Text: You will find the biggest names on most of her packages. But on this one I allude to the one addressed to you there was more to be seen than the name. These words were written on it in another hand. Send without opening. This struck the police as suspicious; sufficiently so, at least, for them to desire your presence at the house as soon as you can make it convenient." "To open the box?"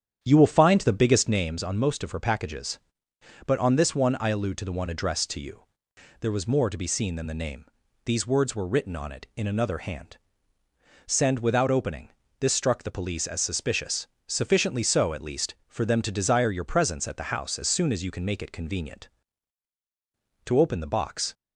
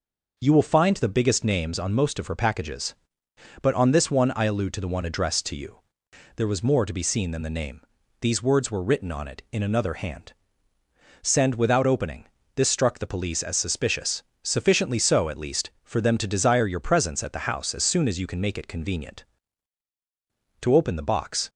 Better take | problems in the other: second | starts louder than the rest; strong; until 1.5 s; 9 dB // pauses between "you" and "there"; noticeable; at 5.6 s; 0.58 s long; noticeable in the second

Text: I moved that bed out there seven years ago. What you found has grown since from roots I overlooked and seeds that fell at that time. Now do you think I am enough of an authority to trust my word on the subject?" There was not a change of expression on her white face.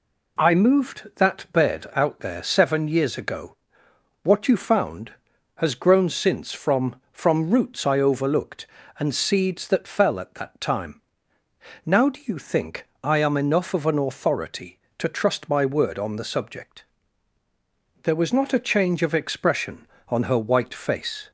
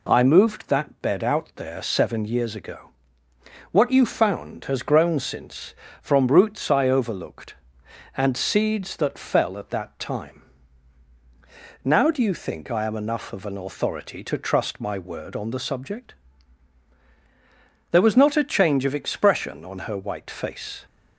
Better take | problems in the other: second | says "from" twice; at 7.1 s // pauses between "think" and "I"; slight; at 12.8 s; 0.16 s long

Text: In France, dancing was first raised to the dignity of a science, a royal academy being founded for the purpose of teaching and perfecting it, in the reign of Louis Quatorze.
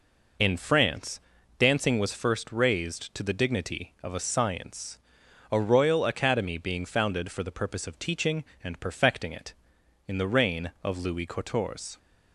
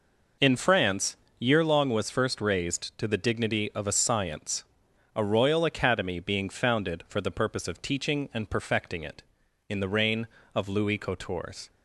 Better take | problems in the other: first | says "yearlong" for "dancing"; at 1.4 s

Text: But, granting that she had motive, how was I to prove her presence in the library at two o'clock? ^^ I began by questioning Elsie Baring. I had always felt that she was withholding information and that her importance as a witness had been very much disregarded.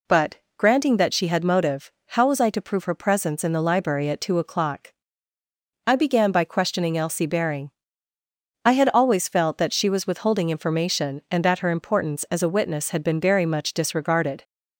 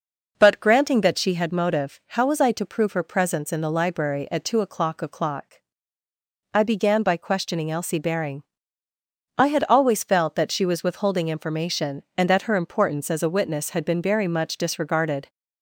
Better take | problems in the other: first | says "o'clock" twice; at 5.0 s

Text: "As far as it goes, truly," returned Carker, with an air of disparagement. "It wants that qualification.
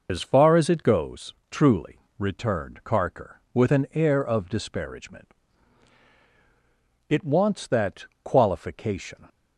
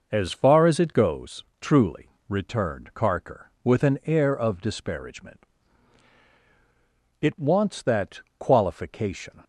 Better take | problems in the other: second | loses the start of "As"; at 0.0 s; 95 ms // pauses between "that" and "qualification"; slight; at 8.0 s; 0.18 s long; slight in the second

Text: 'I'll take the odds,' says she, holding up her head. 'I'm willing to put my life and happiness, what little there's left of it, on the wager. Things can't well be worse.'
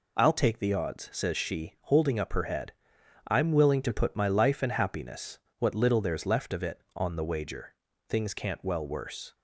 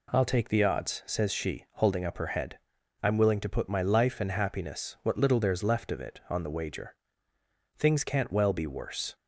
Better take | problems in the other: second | skips "be"; at 8.8 s

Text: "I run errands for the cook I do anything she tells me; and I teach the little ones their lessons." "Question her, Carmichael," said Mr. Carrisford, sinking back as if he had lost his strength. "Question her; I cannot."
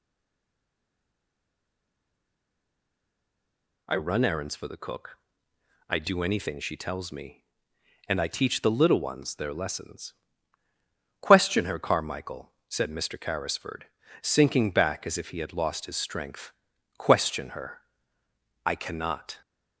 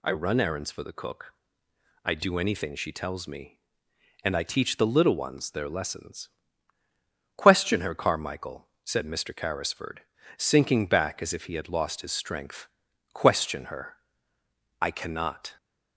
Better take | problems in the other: second | stays silent before the first word; strong; until 3.8 s; 3.8 s long // pauses between "cook" and "I"; noticeable; at 5.1 s; 0.70 s long; noticeable in the second

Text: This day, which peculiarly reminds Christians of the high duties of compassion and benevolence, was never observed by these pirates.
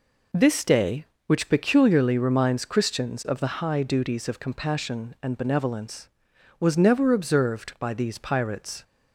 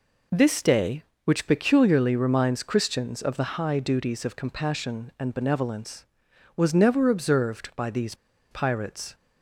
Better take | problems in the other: first | pauses between "these" and "pirates"; at 8.1 s; 0.37 s long

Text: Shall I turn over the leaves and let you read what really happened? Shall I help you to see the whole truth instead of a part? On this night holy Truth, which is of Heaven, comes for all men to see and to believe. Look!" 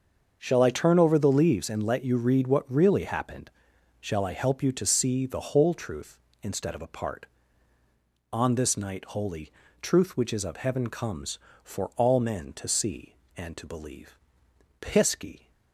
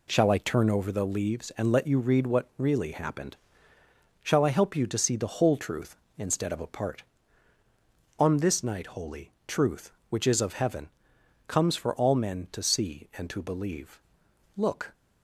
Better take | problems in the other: second | starts louder than the rest; until 1.4 s; 6.5 dB // pauses between "holy" and "Truth"; slight; at 9.5 s; 0.32 s long; slight in the second // says "Pisky" for "Look"; at 14.8 s

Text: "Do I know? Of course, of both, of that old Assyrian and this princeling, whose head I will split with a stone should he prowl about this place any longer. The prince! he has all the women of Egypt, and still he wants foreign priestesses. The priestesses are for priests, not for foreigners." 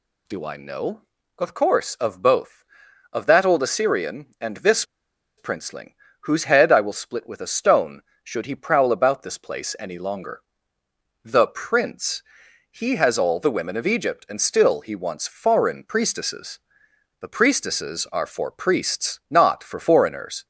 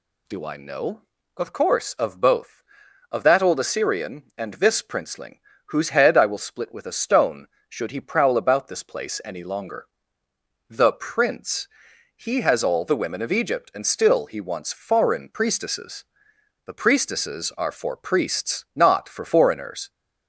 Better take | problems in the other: second | pauses between "this" and "princeling"; noticeable; at 4.8 s; 0.54 s long

